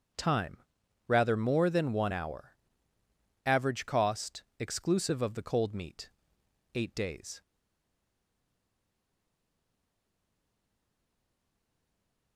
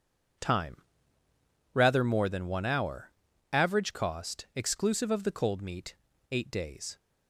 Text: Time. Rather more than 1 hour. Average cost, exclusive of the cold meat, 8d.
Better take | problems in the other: second | starts louder than the rest; until 1.6 s; 6.5 dB // stays silent after the last word; strong; from 7.4 s on; 4.9 s long

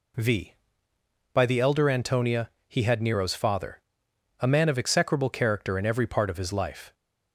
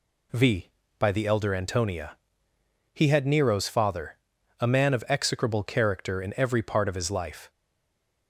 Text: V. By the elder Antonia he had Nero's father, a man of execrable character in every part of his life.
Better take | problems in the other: first | pauses between "Antonia" and "he"; noticeable; at 2.1 s; 0.78 s long; slight in the first // stays silent after the last word; slight; from 7.4 s on; 0.8 s long

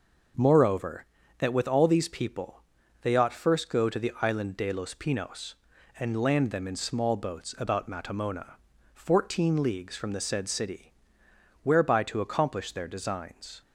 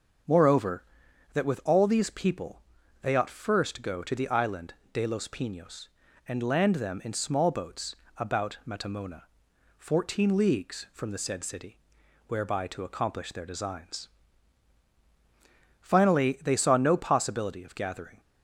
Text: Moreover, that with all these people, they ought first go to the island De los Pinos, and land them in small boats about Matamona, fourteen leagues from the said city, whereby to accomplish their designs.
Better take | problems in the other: first | starts louder than the rest; until 1.8 s; 6.5 dB // pauses between "island" and "De"; slight; at 4.7 s; 0.18 s long // pauses between "boats" and "about"; slight; at 7.9 s; 0.22 s long // goes on to say "Finally they saw no possibility of gathering"; strong; from 15.7 s on; 2.4 s long

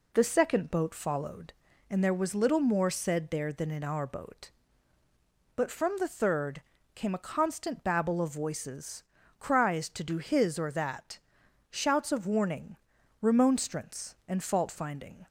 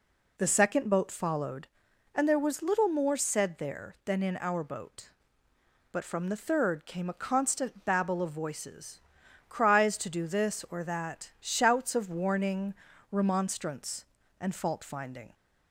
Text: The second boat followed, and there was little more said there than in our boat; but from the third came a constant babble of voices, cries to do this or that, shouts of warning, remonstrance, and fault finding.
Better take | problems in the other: second | pauses between "third" and "came"; slight; at 6.6 s; 0.34 s long // says "his" for "this"; at 10.1 s

